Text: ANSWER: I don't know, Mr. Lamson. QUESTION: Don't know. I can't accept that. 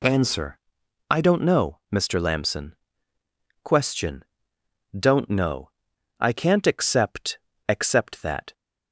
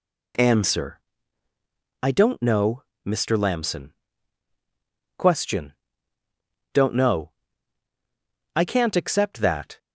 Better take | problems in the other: second | says "accept" twice; at 7.6 s

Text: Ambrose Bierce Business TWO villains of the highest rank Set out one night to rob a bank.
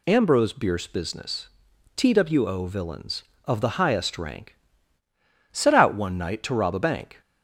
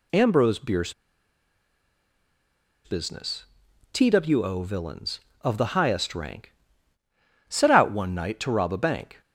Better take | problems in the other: first | pauses between "Bierce" and "Business"; strong; at 0.9 s; 1.9 s long // pauses between "Business" and "TWO"; noticeable; at 3.4 s; 0.48 s long; noticeable in the first // pauses between "rank" and "Set"; noticeable; at 6.5 s; 0.96 s long; noticeable in the first

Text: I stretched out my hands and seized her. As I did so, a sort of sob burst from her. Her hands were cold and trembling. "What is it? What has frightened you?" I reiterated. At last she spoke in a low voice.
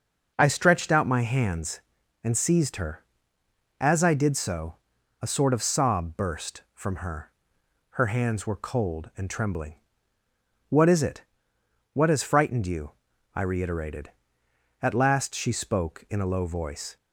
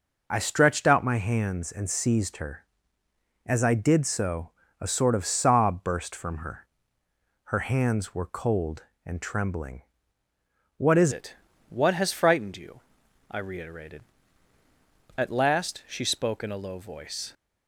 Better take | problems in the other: first | changes voice at "it"; from 11.1 s on; 6.2 s long

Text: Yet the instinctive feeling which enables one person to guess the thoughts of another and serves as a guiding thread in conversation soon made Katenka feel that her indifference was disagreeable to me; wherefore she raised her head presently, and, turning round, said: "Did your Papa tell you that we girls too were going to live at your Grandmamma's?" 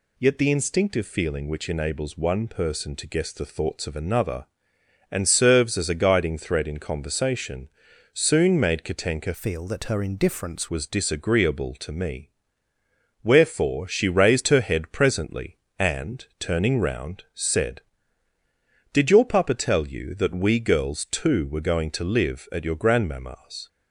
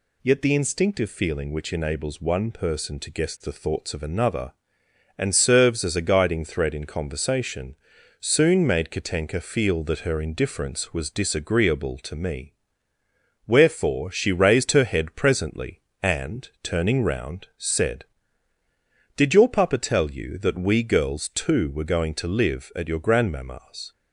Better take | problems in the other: second | pauses between "conversation" and "soon"; noticeable; at 7.6 s; 0.46 s long; noticeable in the second // changes voice from "feel" to "indifference"; from 9.3 to 10.6 s; 1.3 s long

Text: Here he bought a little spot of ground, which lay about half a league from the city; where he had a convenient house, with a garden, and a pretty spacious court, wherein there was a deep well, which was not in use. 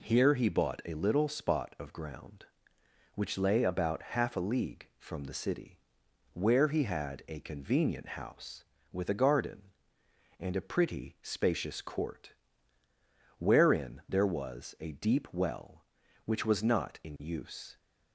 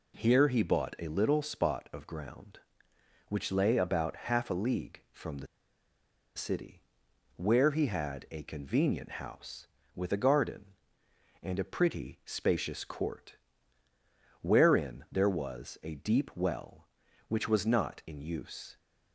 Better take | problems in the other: first | pauses between "the" and "city"; noticeable; at 5.4 s; 0.89 s long

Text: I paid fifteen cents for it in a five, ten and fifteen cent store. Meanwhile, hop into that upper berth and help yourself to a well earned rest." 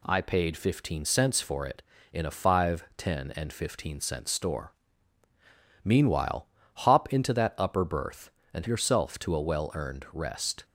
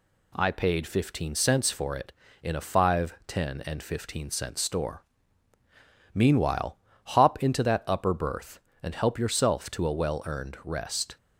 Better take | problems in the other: second | skips "help"; at 8.6 s

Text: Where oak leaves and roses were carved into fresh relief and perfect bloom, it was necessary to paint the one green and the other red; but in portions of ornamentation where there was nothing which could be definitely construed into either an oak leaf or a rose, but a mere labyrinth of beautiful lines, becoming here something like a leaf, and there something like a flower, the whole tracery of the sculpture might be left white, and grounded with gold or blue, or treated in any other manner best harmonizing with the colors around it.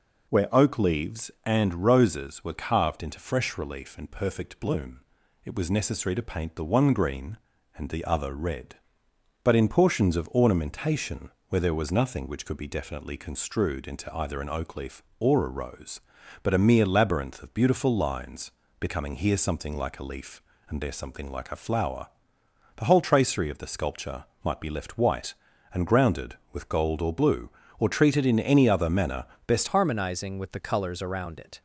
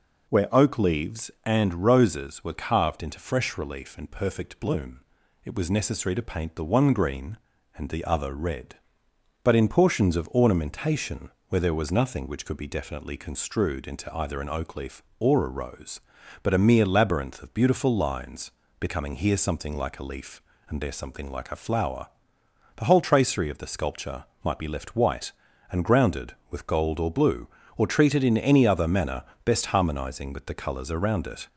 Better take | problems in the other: second | pauses between "ornamentation" and "where"; slight; at 11.2 s; 0.20 s long; slight in the second // pauses between "sculpture" and "might"; slight; at 24.2 s; 0.20 s long; slight in the second // pauses between "manner" and "best"; slight; at 29.2 s; 0.20 s long; slight in the second // changes voice at "harmonizing"; from 29.6 s on; 2.0 s long

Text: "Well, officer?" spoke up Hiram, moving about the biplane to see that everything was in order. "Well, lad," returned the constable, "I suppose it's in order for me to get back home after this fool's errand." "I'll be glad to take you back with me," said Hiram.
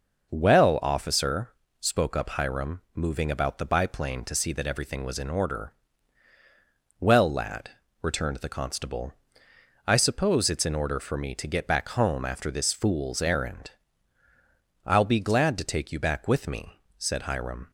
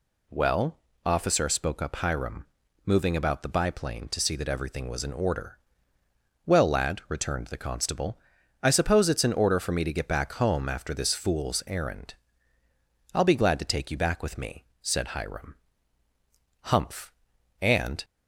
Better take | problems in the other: first | goes on to say "Humph and"; from 16.6 s on; 1.4 s long

